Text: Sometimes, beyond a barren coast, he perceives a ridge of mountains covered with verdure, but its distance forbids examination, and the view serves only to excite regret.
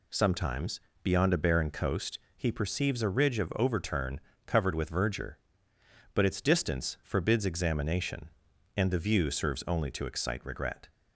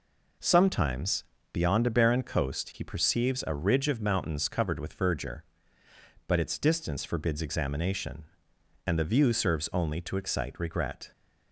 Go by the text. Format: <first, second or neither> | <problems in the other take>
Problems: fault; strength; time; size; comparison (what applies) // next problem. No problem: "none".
second | says "overturn" for "mountains"; at 3.5 s